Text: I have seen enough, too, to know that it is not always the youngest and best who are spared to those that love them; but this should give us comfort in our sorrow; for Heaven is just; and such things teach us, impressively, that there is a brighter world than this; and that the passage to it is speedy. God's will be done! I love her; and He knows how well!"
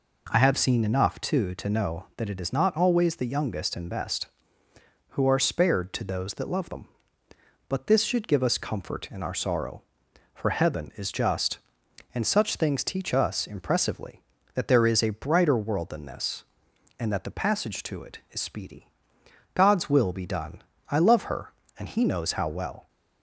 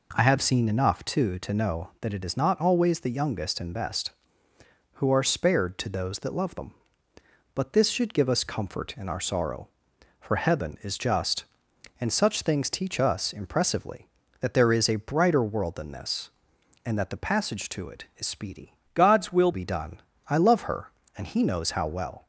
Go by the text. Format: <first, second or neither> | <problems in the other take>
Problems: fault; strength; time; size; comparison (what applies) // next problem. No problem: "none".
first | changes voice from "God's" to "will"; from 18.9 to 19.5 s; 0.6 s long